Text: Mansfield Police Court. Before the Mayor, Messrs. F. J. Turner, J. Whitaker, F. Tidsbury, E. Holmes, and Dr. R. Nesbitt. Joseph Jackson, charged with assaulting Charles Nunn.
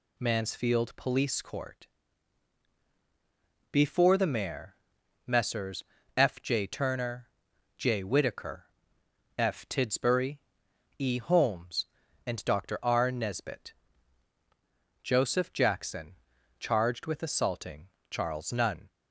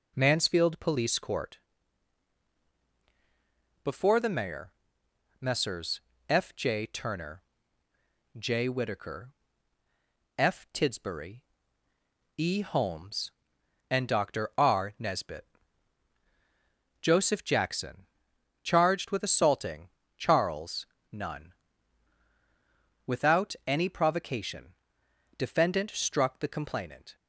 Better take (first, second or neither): first